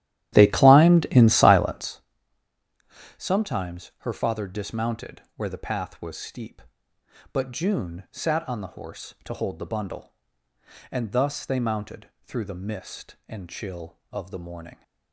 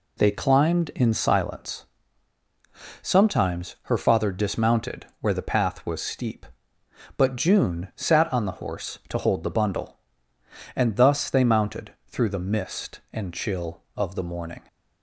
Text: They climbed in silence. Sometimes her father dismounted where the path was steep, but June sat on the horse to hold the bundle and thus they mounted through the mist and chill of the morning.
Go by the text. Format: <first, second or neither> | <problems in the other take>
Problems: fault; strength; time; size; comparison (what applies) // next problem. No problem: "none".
second | starts louder than the rest; strong; until 2.0 s; 12.5 dB // pauses between "mounted" and "through"; slight; at 12.0 s; 0.16 s long; slight in the second